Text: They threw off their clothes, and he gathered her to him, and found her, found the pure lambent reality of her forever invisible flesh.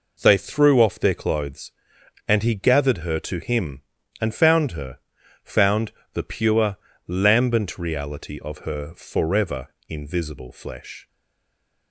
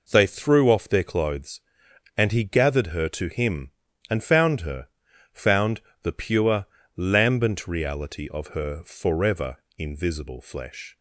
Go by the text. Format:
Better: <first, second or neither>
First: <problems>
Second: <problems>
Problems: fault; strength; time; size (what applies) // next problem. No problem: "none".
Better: second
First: pauses between "found" and "the"; slight; at 5.9 s; 0.22 s long // pauses between "pure" and "lambent"; slight; at 6.7 s; 0.30 s long // pauses between "forever" and "invisible"; slight; at 9.6 s; 0.20 s long // stays silent after the last word; slight; from 11.0 s on; 0.9 s long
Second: pauses between "found" and "the"; slight; at 5.8 s; 0.22 s long // pauses between "pure" and "lambent"; slight; at 6.6 s; 0.30 s long // pauses between "forever" and "invisible"; slight; at 9.5 s; 0.20 s long